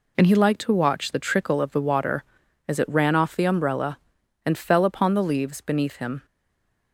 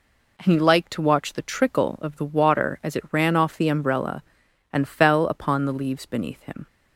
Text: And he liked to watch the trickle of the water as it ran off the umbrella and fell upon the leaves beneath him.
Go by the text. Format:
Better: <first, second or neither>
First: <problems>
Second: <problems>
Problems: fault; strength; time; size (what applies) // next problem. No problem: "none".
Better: second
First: stays silent after the last word; slight; from 6.2 s on; 0.7 s long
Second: none